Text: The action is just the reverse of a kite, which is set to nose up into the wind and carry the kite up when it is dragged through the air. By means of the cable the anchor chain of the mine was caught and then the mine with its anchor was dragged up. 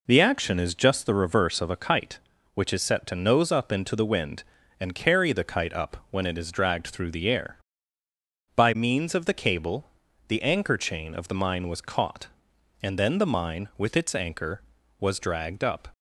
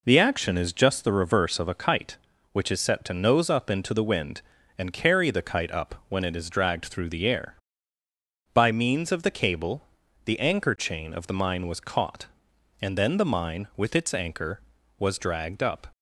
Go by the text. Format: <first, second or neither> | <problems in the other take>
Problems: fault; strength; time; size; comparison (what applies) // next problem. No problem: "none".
neither | pauses between "cable" and "the"; the same in both